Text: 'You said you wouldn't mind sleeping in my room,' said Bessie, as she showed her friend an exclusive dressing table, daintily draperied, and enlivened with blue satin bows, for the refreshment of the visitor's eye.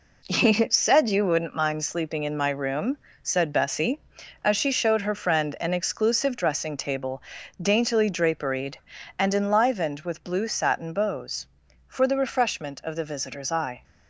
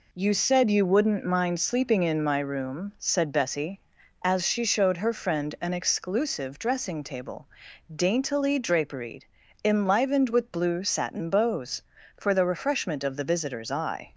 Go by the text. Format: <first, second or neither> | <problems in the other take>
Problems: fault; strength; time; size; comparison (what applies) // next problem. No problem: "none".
first | skips "and"; at 9.4 s